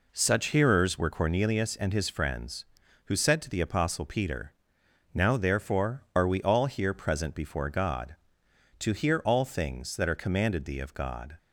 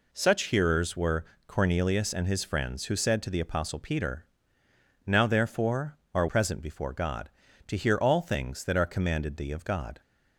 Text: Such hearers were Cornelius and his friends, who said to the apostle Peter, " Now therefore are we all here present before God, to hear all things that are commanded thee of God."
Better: first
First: none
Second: pauses between "were" and "Cornelius"; slight; at 1.2 s; 0.22 s long // skips "we all here"; at 6.2 s

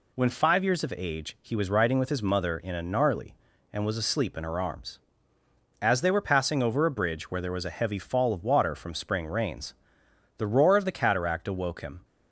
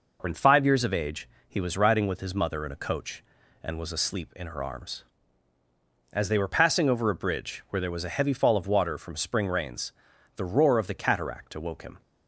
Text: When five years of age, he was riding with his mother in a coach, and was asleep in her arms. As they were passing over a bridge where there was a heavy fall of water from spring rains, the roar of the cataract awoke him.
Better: second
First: says "gnarly" for "coach"; at 2.8 s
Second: none

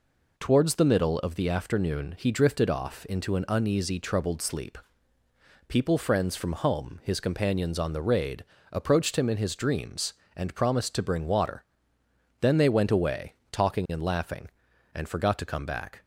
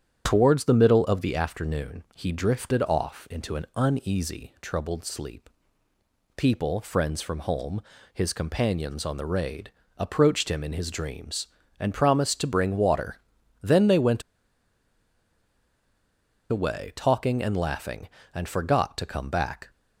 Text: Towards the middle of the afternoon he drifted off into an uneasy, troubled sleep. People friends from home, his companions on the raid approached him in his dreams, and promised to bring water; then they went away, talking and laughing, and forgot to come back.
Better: first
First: pauses between "raid" and "approached"; slight; at 8.4 s; 0.26 s long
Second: starts louder than the rest; strong; until 1.2 s; 9 dB // pauses between "raid" and "approached"; slight; at 9.7 s; 0.26 s long // pauses between "went" and "away"; strong; at 14.2 s; 2.2 s long

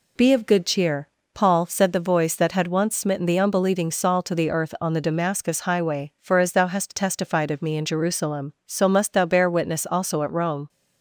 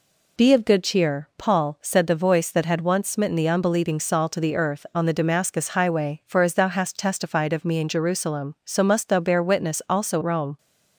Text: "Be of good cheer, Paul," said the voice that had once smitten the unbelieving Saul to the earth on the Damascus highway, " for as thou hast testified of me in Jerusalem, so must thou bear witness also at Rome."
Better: first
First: none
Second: skips "at"; at 10.2 s

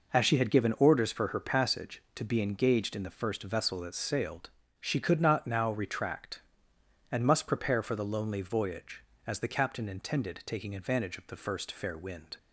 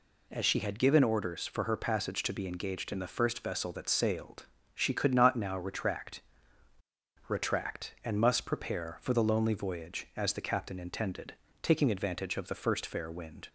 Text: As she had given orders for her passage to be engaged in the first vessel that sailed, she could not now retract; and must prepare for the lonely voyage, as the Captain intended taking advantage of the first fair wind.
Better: first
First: none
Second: says "retract" twice; at 7.2 s // pauses between "intended" and "taking"; slight; at 11.3 s; 0.28 s long

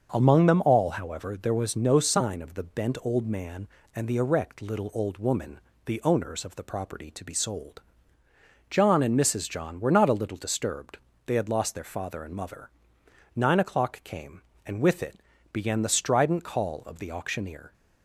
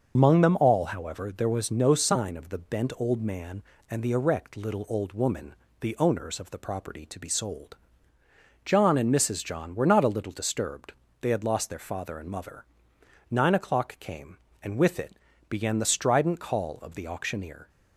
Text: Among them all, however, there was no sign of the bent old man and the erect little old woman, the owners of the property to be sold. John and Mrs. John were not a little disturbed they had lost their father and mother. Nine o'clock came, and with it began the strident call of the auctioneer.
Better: first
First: starts louder than the rest; until 1.1 s; 6.5 dB // pauses between "disturbed" and "they"; slight; at 10.9 s; 0.28 s long // pauses between "it" and "began"; slight; at 15.2 s; 0.32 s long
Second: loses the start of "Among"; at 0.1 s; 105 ms // starts louder than the rest; until 1.1 s; 6.5 dB // pauses between "disturbed" and "they"; slight; at 10.9 s; 0.28 s long // pauses between "it" and "began"; slight; at 15.1 s; 0.32 s long

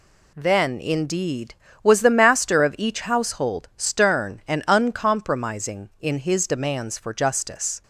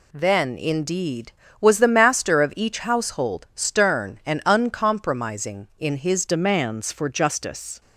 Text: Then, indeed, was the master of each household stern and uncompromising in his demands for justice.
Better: first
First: none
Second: changes voice at "demands"; from 6.2 s on; 1.6 s long

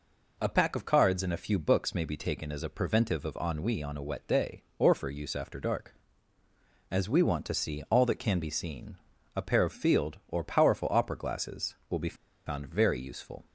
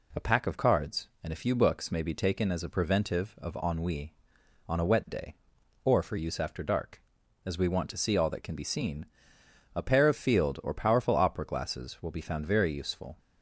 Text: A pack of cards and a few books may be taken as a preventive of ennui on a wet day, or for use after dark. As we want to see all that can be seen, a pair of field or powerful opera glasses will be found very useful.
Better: second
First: pauses between "be" and "found"; slight; at 12.1 s; 0.30 s long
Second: none

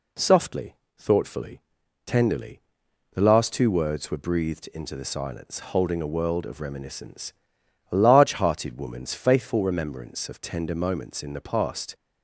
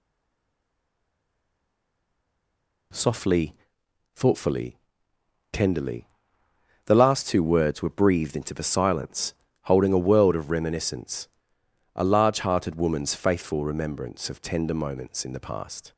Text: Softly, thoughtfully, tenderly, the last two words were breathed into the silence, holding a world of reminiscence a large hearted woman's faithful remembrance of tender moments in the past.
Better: first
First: pauses between "reminiscence" and "a"; noticeable; at 7.3 s; 0.58 s long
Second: stays silent before the first word; strong; until 2.9 s; 2.9 s long // pauses between "reminiscence" and "a"; noticeable; at 11.2 s; 0.66 s long

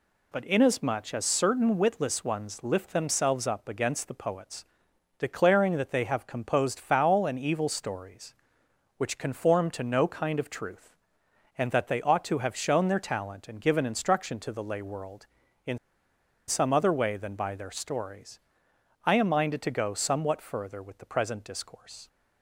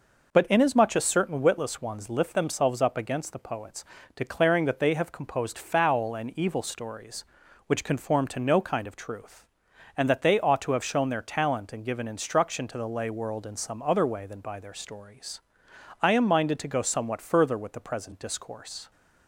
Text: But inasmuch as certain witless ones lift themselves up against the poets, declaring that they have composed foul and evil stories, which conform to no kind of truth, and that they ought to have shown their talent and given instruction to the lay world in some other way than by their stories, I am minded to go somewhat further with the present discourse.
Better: second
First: pauses between "in" and "some"; noticeable; at 15.7 s; 0.71 s long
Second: none

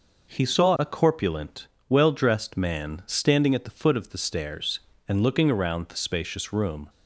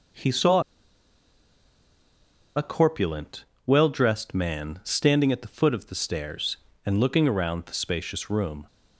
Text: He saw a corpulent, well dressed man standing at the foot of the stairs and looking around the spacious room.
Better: first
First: none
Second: pauses between "saw" and "a"; strong; at 0.6 s; 1.9 s long

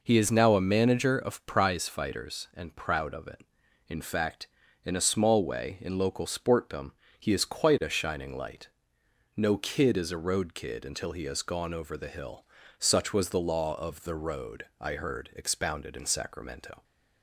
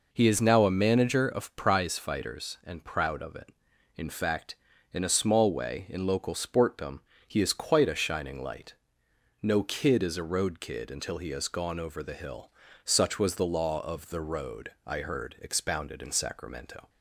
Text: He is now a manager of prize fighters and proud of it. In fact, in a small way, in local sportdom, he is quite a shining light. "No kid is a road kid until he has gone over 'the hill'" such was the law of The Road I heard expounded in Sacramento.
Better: neither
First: pauses between "hill" and "such"; slight; at 12.4 s; 0.32 s long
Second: pauses between "hill" and "such"; slight; at 12.5 s; 0.32 s long

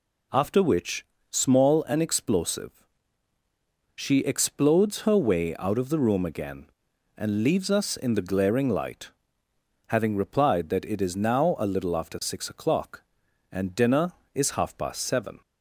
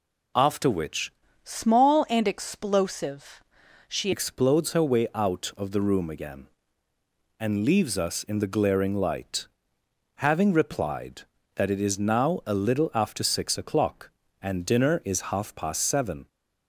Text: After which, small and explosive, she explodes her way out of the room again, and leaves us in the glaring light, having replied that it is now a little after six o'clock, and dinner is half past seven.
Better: first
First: none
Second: changes voice from "small" to "she"; from 1.4 to 4.1 s; 2.7 s long

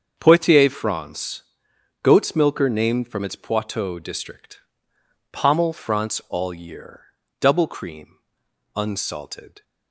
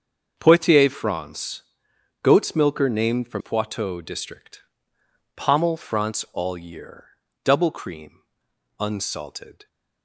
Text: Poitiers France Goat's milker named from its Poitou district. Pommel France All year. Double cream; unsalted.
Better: first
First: starts louder than the rest; until 1.2 s; 7 dB // pauses between "France" and "Goat's"; noticeable; at 1.4 s; 0.58 s long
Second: starts louder than the rest; until 1.4 s; 7 dB // pauses between "France" and "Goat's"; noticeable; at 1.6 s; 0.58 s long // skips "its"; at 3.4 s

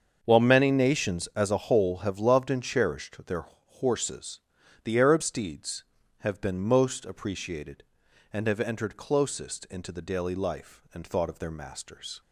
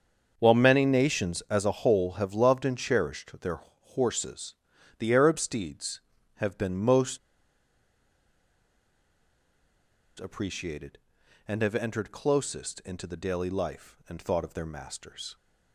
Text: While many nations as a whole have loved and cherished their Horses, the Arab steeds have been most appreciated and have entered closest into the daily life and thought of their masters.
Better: first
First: starts louder than the rest; until 1.2 s; 7 dB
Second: starts louder than the rest; until 1.3 s; 7 dB // pauses between "most" and "appreciated"; strong; at 7.1 s; 3.0 s long

